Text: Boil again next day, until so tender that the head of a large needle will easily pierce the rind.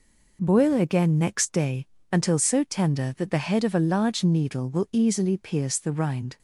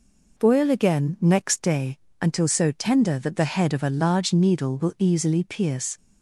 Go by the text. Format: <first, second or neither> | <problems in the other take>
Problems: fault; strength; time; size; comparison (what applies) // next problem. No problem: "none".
first | stops before "the rind"; at 5.9 s